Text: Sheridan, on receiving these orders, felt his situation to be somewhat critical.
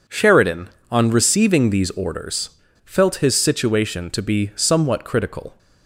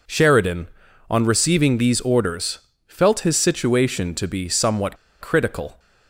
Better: first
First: none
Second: pauses between "somewhat" and "critical"; slight; at 4.9 s; 0.24 s long

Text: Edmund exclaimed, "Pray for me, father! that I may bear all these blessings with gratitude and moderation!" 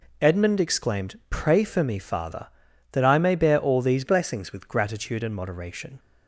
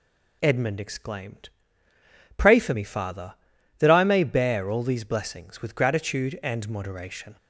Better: second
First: changes voice from "blessings" to "with"; from 4.0 to 4.6 s; 0.6 s long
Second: none

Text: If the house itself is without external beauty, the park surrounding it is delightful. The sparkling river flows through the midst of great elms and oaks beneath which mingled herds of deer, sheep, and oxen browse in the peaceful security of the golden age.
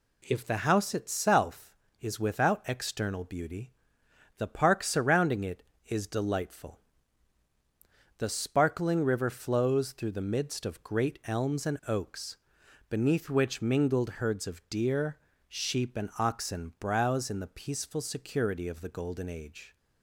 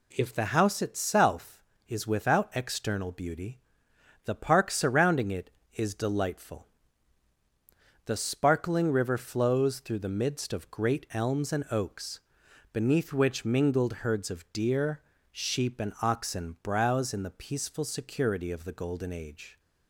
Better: neither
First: pauses between "oaks" and "beneath"; noticeable; at 12.3 s; 0.50 s long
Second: pauses between "oaks" and "beneath"; noticeable; at 12.2 s; 0.50 s long

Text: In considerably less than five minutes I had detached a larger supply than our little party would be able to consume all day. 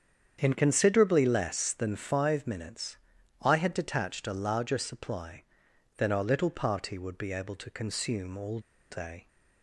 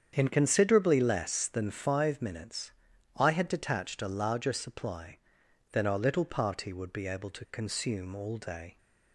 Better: second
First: starts louder than the rest; strong; until 1.4 s; 8 dB // pauses between "minutes" and "I"; noticeable; at 2.9 s; 0.46 s long // pauses between "all" and "day"; slight; at 8.5 s; 0.30 s long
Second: starts louder than the rest; strong; until 1.1 s; 8 dB // pauses between "minutes" and "I"; noticeable; at 2.7 s; 0.46 s long

